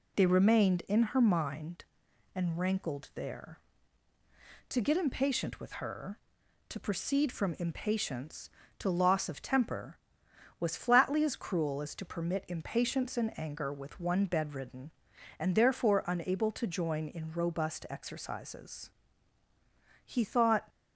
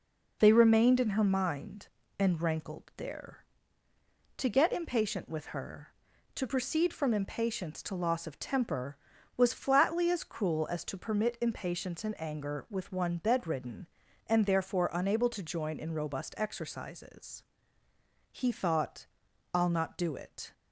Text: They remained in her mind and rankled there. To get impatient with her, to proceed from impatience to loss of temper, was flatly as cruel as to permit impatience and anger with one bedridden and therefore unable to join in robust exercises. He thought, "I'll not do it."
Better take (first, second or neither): second